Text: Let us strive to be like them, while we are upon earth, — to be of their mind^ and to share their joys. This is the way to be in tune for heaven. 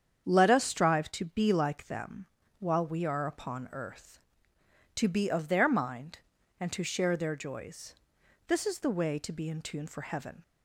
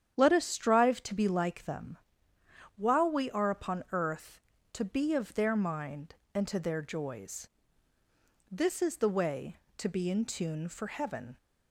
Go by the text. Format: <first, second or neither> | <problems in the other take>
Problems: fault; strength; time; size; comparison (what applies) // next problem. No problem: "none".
first | starts louder than the rest; strong; until 1.1 s; 9.5 dB; strong in the first // skips "share"; at 6.5 s